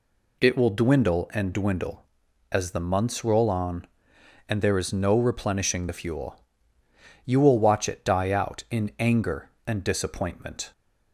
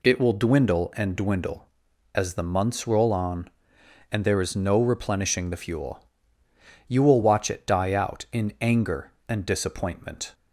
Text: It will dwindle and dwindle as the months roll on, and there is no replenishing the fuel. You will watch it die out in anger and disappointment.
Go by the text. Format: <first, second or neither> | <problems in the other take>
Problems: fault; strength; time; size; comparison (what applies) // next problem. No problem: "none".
neither | none